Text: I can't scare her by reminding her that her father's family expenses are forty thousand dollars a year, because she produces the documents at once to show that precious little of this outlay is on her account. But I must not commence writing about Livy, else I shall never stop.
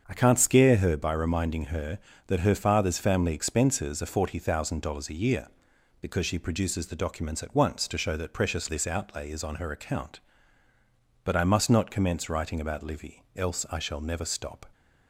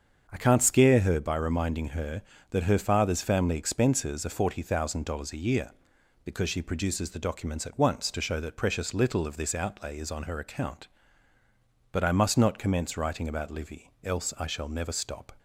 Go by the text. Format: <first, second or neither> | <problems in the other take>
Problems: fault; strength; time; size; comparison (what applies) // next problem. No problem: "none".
second | starts louder than the rest; until 1.0 s; 7 dB; also in the second // skips "little of"; at 8.6 s